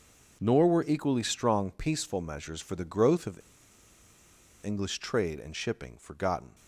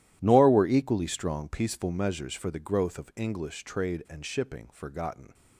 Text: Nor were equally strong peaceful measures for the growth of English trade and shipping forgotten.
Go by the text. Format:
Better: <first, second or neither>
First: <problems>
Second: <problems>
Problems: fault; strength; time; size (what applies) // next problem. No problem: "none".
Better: second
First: pauses between "of" and "English"; at 3.4 s; 1.2 s long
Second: none